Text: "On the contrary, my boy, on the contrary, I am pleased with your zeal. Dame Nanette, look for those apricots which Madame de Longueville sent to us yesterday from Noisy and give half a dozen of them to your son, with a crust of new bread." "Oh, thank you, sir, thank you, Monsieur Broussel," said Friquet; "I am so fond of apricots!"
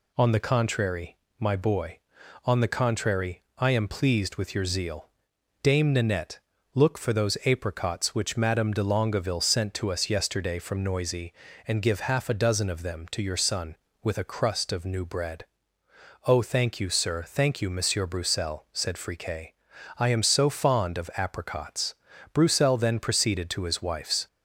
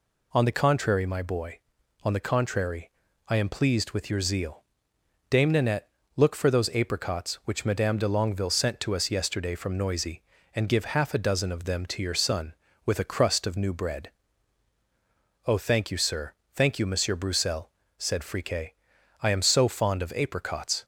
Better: second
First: goes on to say "Broussel then proceeded to his wife's"; strong; from 22.3 s on; 1.9 s long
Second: none

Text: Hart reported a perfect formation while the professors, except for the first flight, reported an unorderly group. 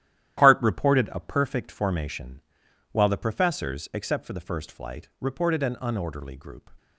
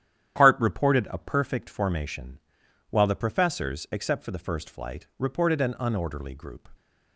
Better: second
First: gets quieter; strong; throughout; 9 dB // starts louder than the rest; strong; until 1.4 s; 12 dB // pauses between "formation" and "while"; noticeable; at 2.4 s; 0.52 s long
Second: starts louder than the rest; strong; until 1.3 s; 10 dB // pauses between "formation" and "while"; noticeable; at 2.3 s; 0.52 s long

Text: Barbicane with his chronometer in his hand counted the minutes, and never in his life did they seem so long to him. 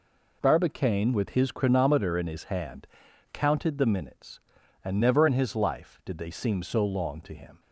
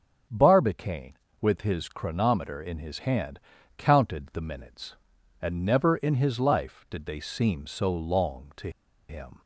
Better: first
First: pauses between "hand" and "counted"; noticeable; at 2.8 s; 0.46 s long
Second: starts louder than the rest; noticeable; until 1.5 s; 6 dB // pauses between "hand" and "counted"; slight; at 3.3 s; 0.36 s long // pauses between "to" and "him"; at 8.6 s; 0.39 s long

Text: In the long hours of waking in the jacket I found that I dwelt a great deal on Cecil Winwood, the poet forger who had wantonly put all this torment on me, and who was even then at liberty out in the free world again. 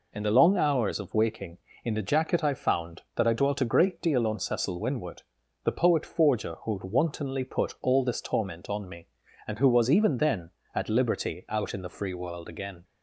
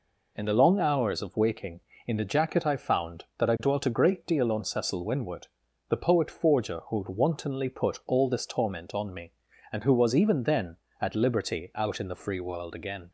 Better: neither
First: none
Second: none

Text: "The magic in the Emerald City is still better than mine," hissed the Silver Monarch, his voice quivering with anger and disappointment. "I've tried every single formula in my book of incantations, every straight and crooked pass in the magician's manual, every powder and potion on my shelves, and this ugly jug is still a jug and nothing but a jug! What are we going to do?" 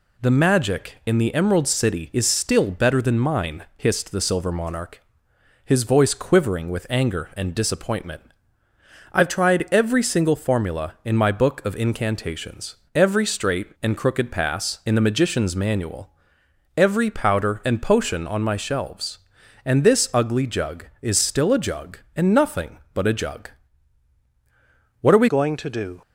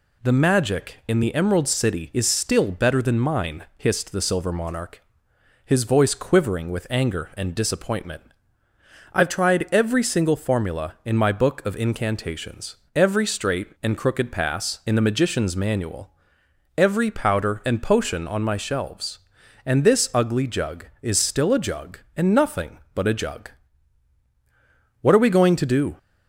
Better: second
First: changes voice at "going"; from 25.2 s on; 0.8 s long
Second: none

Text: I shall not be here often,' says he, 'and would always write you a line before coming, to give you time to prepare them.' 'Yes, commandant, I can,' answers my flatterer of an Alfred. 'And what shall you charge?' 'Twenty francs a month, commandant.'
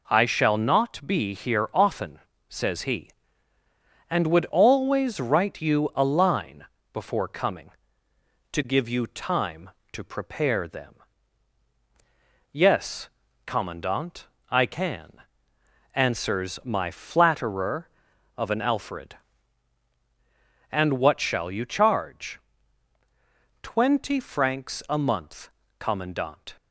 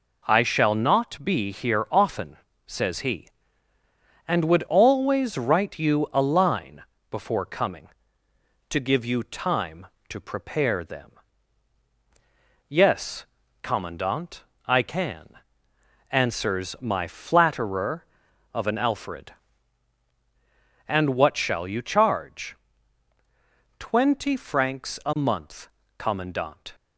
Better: neither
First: pauses between "line" and "before"; slight; at 6.6 s; 0.28 s long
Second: pauses between "line" and "before"; slight; at 6.8 s; 0.28 s long

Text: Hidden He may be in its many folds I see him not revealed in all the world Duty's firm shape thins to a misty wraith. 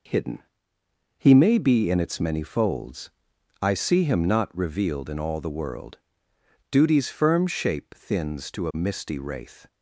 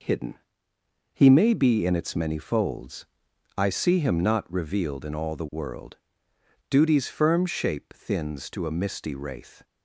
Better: neither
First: pauses between "Hidden" and "He"; noticeable; at 0.3 s; 0.80 s long // pauses between "folds" and "I"; noticeable; at 3.1 s; 0.50 s long // pauses between "world" and "Duty's"; noticeable; at 5.9 s; 0.72 s long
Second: pauses between "Hidden" and "He"; noticeable; at 0.3 s; 0.80 s long // pauses between "folds" and "I"; noticeable; at 3.0 s; 0.50 s long // pauses between "world" and "Duty's"; noticeable; at 5.9 s; 0.72 s long

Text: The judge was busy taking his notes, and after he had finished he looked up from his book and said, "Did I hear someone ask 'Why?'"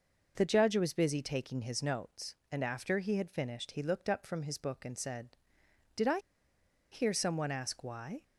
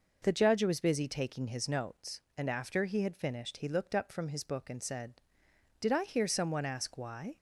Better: second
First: pauses between "I" and "hear"; noticeable; at 6.1 s; 0.73 s long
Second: none

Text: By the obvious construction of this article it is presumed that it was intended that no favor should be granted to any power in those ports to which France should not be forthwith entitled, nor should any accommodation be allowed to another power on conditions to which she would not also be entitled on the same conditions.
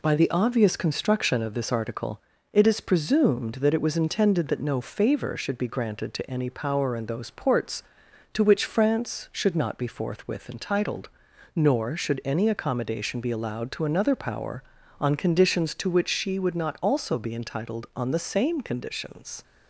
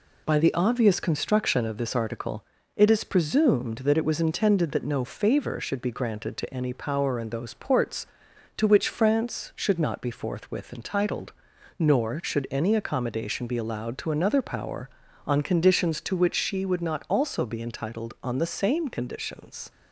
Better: neither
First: pauses between "article" and "it"; slight; at 2.1 s; 0.32 s long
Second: pauses between "article" and "it"; slight; at 2.4 s; 0.32 s long

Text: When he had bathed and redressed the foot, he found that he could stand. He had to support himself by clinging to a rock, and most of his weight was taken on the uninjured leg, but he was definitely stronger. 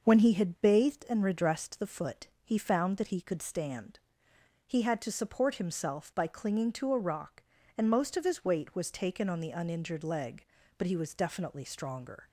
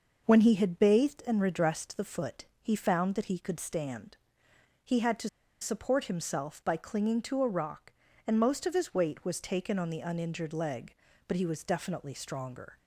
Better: first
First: none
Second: pauses between "to" and "support"; slight; at 5.2 s; 0.32 s long

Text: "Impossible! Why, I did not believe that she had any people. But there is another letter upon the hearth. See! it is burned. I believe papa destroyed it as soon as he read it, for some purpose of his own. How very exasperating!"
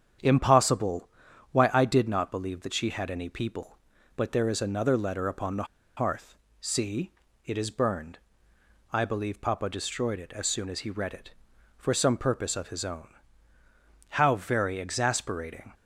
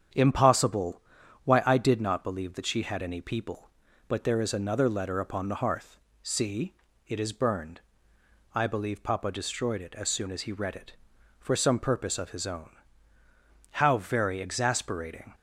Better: second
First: starts louder than the rest; strong; until 1.6 s; 8.5 dB // pauses between "the" and "hearth"; slight; at 5.6 s; 0.32 s long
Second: starts louder than the rest; strong; until 1.5 s; 8 dB

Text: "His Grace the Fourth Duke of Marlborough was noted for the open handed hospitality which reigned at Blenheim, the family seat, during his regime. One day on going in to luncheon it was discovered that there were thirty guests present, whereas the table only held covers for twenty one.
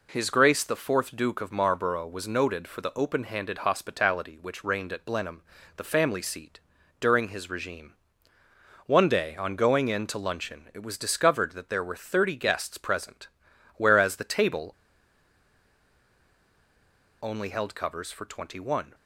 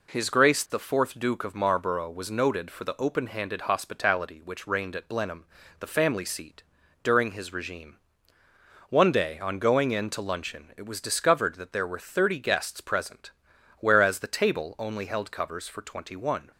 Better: second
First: pauses between "table" and "only"; strong; at 14.7 s; 2.4 s long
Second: none

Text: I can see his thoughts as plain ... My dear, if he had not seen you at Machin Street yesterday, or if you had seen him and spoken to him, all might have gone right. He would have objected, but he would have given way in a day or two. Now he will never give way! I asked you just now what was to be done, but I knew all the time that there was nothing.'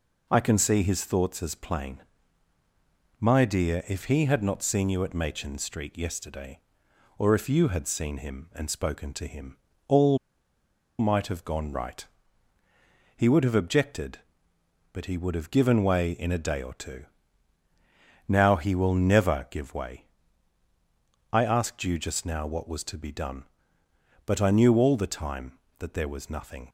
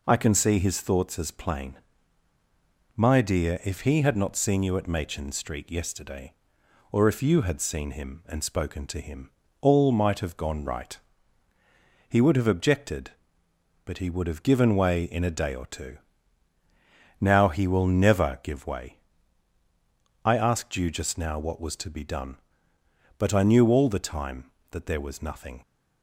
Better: second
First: pauses between "all" and "might"; noticeable; at 10.1 s; 0.81 s long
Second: none

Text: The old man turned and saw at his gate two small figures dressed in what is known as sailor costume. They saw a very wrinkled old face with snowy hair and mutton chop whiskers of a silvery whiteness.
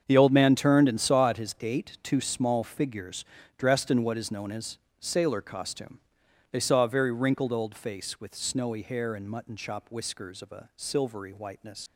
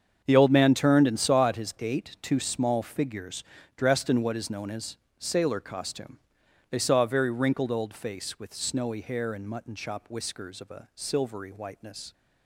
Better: second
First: starts louder than the rest; strong; until 1.0 s; 7 dB // pauses between "figures" and "dressed"; slight; at 3.2 s; 0.34 s long // pauses between "as" and "sailor"; slight; at 4.7 s; 0.22 s long // leaves "whiteness" unfinished; at 11.8 s; 75 ms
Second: starts louder than the rest; strong; until 1.2 s; 7 dB // pauses between "figures" and "dressed"; slight; at 3.4 s; 0.34 s long // pauses between "as" and "sailor"; slight; at 4.9 s; 0.22 s long

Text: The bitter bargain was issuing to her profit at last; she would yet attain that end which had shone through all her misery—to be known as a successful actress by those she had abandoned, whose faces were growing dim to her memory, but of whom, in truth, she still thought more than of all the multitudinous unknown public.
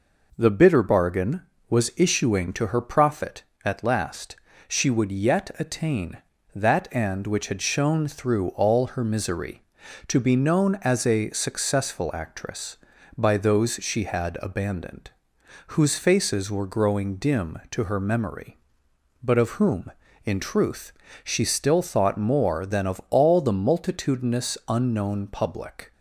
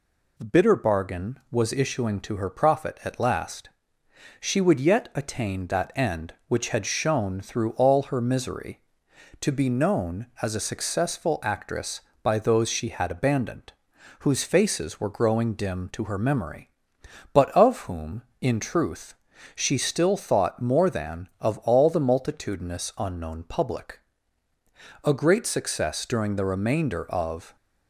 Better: first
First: none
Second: goes on to say "A great success during the remainder of"; strong; from 25.0 s on; 2.5 s long

